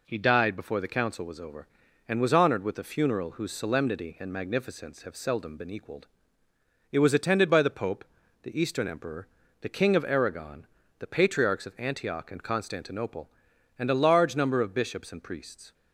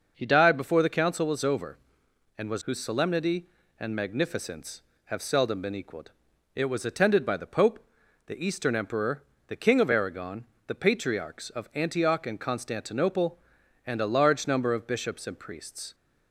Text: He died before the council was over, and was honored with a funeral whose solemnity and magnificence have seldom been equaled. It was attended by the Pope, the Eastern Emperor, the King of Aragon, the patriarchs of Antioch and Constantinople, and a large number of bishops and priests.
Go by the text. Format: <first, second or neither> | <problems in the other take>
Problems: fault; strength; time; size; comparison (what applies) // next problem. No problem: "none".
first | starts louder than the rest; noticeable; until 1.1 s; 6 dB // skips "honored with a funeral"; at 2.6 s